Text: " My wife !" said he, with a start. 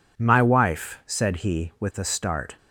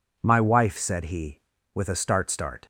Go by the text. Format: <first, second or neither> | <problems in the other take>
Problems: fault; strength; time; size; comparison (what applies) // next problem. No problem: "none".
first | says "start" twice; at 2.3 s